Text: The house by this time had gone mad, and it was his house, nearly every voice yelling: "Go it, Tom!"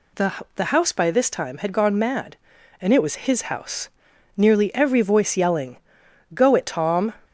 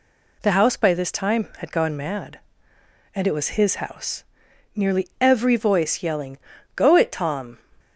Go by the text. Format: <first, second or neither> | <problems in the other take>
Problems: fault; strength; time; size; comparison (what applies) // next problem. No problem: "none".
second | says "The" twice; at 0.5 s